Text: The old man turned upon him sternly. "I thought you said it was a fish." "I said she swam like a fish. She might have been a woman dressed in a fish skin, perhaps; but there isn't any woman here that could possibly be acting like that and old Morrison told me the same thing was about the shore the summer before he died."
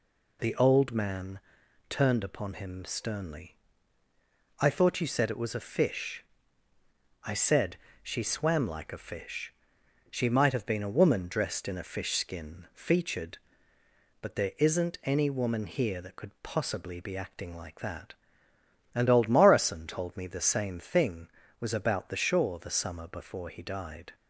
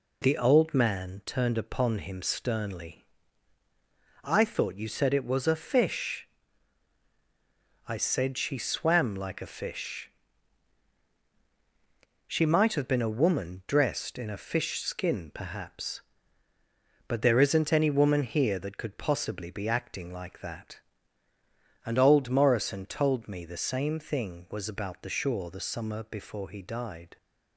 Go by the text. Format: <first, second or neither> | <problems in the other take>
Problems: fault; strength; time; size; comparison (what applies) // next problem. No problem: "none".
second | pauses between "man" and "turned"; noticeable; at 1.3 s; 0.52 s long // pauses between "said" and "she"; slight; at 7.7 s; 0.26 s long // says "featured" for "perhaps"; at 12.7 s